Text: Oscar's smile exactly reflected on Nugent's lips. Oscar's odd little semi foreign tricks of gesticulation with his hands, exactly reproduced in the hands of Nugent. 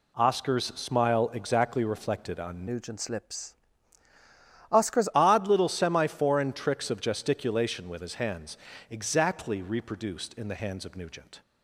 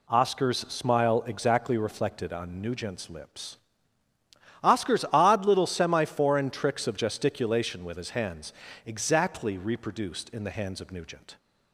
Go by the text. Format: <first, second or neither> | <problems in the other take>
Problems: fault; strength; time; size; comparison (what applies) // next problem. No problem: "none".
second | changes voice from "Nugent's" to "Oscar's"; from 2.6 to 5.0 s; 2.4 s long